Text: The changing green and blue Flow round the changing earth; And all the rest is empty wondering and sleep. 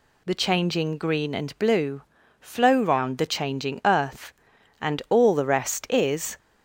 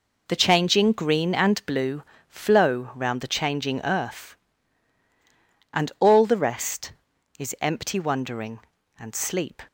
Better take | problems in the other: second | pauses between "blue" and "Flow"; at 2.0 s; 0.38 s long; slight in the second // stops before "empty wondering and sleep"; at 6.3 s

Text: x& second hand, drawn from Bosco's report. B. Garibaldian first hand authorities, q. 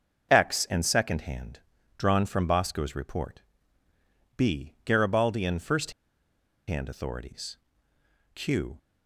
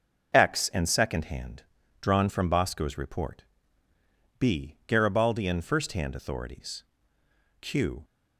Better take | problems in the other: second | starts louder than the rest; noticeable; until 1.3 s; 6 dB // pauses between "first" and "hand"; noticeable; at 5.9 s; 0.76 s long

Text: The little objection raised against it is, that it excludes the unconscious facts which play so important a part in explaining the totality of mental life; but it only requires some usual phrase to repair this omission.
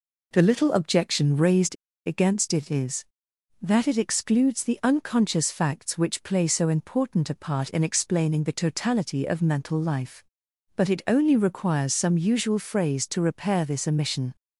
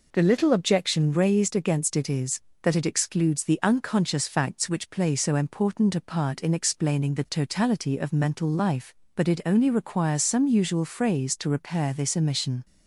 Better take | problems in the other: second | pauses between "raised" and "against"; slight; at 1.7 s; 0.30 s long

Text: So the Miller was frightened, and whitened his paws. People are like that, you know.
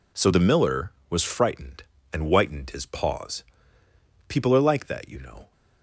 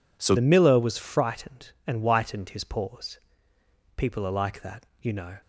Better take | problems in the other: first | changes voice at "the"; from 0.3 s on; 5.0 s long

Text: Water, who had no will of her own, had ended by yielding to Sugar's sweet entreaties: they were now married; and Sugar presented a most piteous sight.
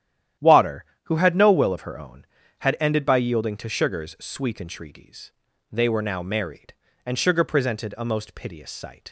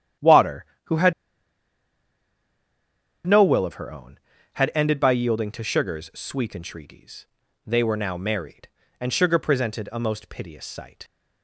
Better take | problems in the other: first | starts louder than the rest; strong; until 3.5 s; 11 dB; strong in the first // pauses between "had" and "no"; strong; at 1.1 s; 2.1 s long

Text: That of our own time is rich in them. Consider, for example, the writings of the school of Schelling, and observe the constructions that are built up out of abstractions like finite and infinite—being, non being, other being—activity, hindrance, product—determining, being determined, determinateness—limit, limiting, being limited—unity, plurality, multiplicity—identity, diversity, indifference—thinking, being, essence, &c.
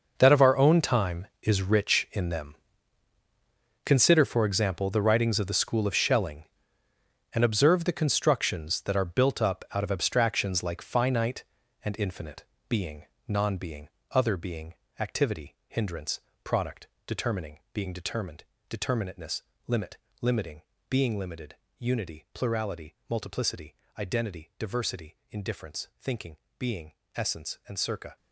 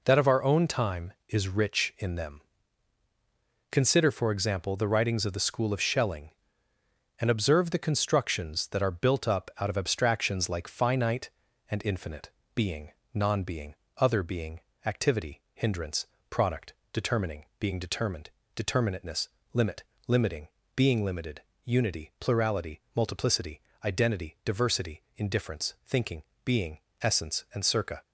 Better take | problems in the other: second | gets quieter; strong; throughout; 14 dB

